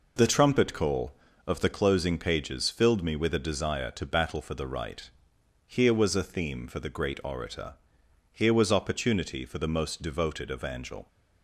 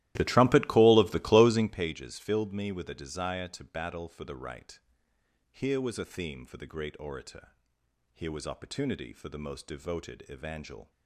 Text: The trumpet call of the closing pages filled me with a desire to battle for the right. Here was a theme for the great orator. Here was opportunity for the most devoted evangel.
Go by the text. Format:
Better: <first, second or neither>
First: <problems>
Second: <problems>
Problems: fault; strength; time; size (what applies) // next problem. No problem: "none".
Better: first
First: none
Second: starts louder than the rest; strong; until 1.8 s; 15 dB